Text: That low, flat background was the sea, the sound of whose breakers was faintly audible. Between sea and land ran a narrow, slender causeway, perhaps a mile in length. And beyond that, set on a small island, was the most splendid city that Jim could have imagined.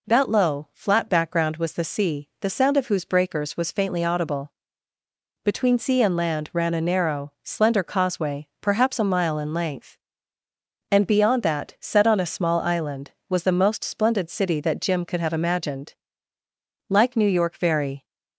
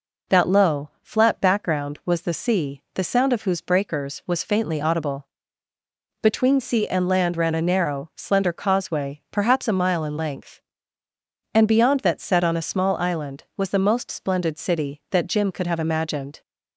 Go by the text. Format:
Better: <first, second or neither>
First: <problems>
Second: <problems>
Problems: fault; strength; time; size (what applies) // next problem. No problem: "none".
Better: second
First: goes on to say "Like New York very"; noticeable; from 16.9 s on; 1.1 s long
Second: none